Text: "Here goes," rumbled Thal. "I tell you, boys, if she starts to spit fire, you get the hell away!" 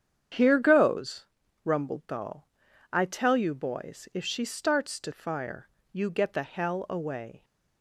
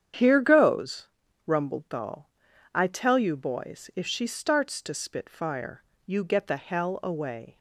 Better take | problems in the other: second | starts louder than the rest; strong; until 1.7 s; 8.5 dB; strong in the second // skips "spit"; at 5.1 s

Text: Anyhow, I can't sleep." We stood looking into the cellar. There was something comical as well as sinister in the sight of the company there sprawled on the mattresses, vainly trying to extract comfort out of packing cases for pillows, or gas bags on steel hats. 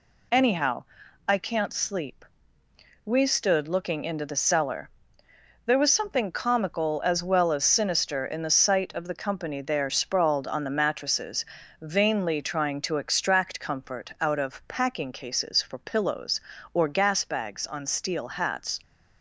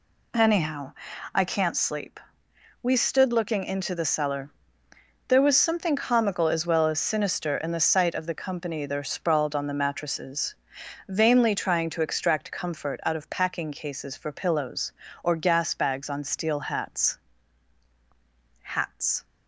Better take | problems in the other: first | says "hats" twice; at 18.6 s

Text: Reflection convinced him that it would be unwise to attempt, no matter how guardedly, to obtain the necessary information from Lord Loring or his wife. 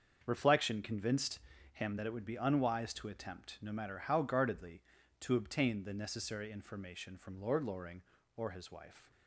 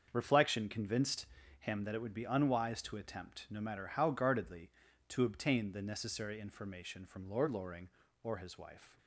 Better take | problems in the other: neither | starts louder than the rest; the same in both // pauses between "convinced" and "him"; slight; the same in both

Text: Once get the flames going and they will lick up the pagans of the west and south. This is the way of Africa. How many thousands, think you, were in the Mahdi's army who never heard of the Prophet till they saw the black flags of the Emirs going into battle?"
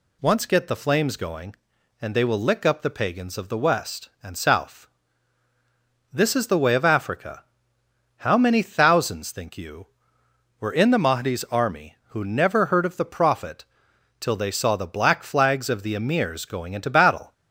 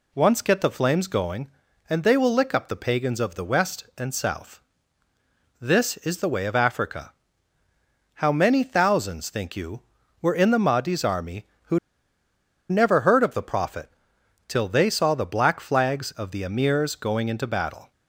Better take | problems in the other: first | pauses between "who" and "never"; noticeable; at 11.7 s; 0.92 s long // pauses between "Prophet" and "till"; noticeable; at 13.8 s; 0.58 s long; noticeable in the first

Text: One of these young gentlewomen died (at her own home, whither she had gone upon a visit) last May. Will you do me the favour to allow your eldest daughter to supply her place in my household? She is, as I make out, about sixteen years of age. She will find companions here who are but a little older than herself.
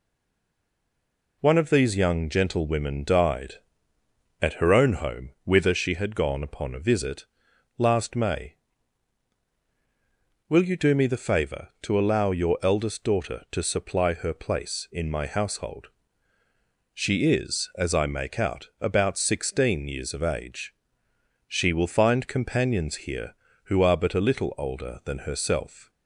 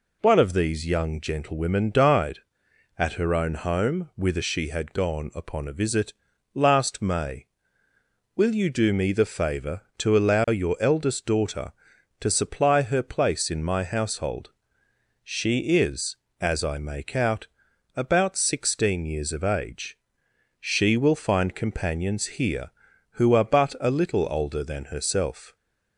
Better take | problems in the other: second | stays silent before the first word; noticeable; until 1.4 s; 1.4 s long

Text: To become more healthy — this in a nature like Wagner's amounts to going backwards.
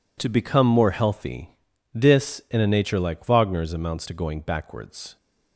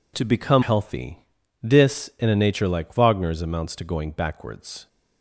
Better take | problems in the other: first | skips "more"; at 0.6 s

